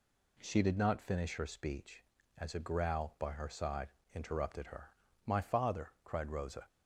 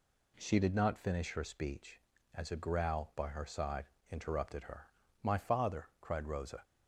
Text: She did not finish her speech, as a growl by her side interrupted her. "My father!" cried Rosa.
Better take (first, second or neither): neither